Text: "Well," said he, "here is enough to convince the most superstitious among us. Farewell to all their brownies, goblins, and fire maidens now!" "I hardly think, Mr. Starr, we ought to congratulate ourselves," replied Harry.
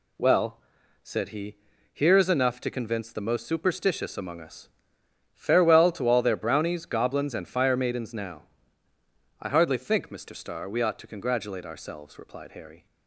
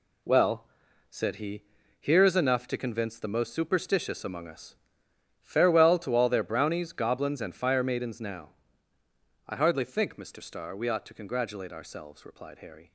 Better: first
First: none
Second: gets quieter; strong; throughout; 8.5 dB

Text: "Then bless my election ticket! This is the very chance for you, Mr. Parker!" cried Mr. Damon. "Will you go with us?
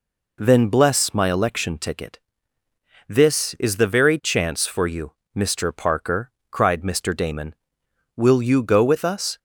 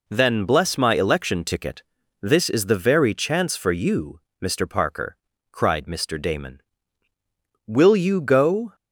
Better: first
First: none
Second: stops before "with us"; at 8.7 s

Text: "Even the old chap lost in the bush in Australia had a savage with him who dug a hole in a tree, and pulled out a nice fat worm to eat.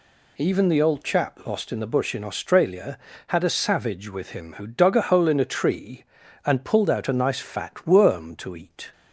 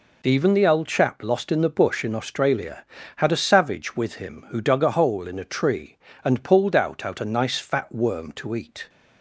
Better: first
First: none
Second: says "out" twice; at 7.0 s

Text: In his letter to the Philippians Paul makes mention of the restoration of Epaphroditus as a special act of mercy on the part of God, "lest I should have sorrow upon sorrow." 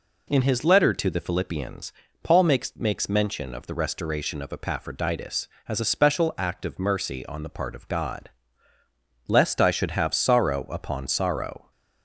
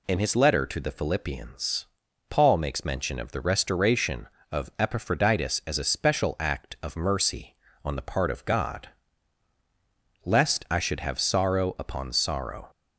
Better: second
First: pauses between "Philippians" and "Paul"; slight; at 1.9 s; 0.32 s long // says "makes" twice; at 2.7 s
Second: pauses between "Philippians" and "Paul"; at 1.8 s; 0.42 s long

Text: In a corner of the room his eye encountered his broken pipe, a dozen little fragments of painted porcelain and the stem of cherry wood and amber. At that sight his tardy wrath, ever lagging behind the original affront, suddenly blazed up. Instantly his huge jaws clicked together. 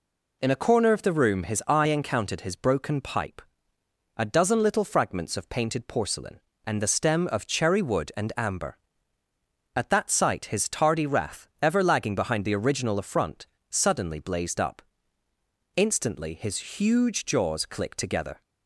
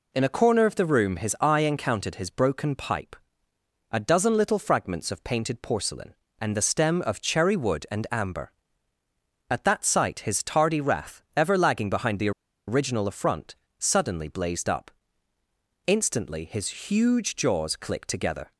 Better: first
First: none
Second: pauses between "the" and "original"; at 12.3 s; 0.37 s long

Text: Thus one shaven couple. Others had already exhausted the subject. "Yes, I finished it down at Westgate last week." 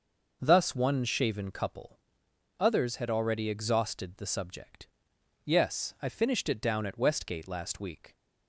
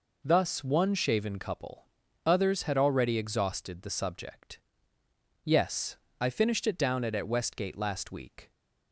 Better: first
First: none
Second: says "at" twice; at 7.1 s

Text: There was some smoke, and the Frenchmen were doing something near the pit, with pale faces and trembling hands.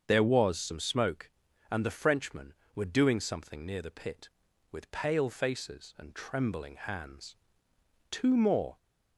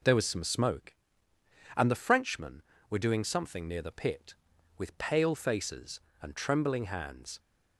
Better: second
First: starts louder than the rest; until 1.0 s; 7 dB // goes on to say "Two more"; noticeable; from 8.0 s on; 0.66 s long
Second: none

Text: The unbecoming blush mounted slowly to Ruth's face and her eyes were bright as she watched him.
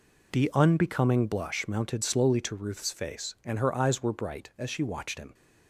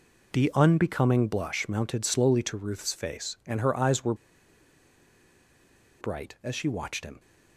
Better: first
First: none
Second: pauses between "were" and "bright"; strong; at 4.1 s; 1.8 s long

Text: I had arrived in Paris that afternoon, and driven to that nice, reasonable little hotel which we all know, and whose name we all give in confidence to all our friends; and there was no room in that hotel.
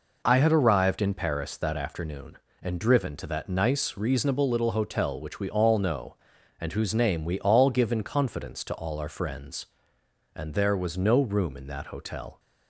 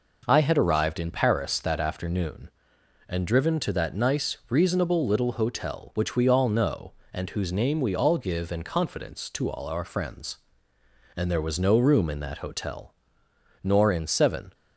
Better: first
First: none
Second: goes on to say "Nor in seven"; noticeable; from 13.6 s on; 0.92 s long

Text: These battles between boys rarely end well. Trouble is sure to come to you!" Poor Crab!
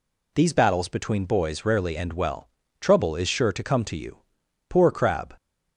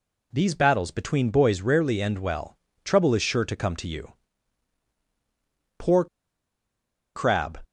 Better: first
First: none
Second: pauses between "Poor" and "Crab"; at 6.0 s; 1.0 s long

